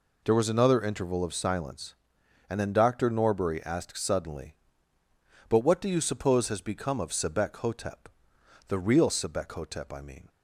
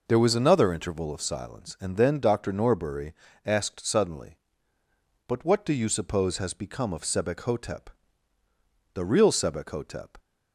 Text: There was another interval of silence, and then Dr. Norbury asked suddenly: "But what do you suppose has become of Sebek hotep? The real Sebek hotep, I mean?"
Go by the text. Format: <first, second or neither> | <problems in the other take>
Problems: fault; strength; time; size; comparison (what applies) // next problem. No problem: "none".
first | pauses between "Norbury" and "asked"; slight; at 3.1 s; 0.32 s long // stops before "I mean"; at 10.1 s